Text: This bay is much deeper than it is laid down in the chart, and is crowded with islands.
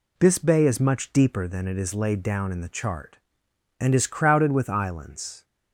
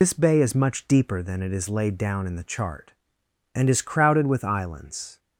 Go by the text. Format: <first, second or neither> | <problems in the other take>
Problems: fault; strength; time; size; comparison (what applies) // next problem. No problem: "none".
first | loses the start of "This"; at 0.0 s; 85 ms